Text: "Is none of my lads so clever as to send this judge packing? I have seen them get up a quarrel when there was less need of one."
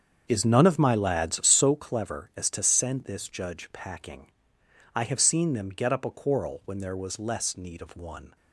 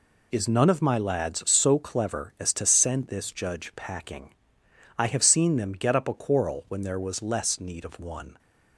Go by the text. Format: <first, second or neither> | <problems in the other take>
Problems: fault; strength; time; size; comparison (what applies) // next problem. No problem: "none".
second | starts louder than the rest; strong; until 1.7 s; 7.5 dB